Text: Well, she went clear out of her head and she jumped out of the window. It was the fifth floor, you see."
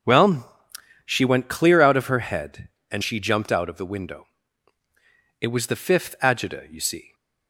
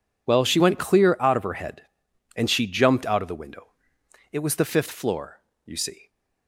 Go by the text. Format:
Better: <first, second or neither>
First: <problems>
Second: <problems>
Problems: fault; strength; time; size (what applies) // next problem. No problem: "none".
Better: second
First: starts louder than the rest; noticeable; until 1.5 s; 6 dB // says "agita" for "floor"; at 6.2 s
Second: none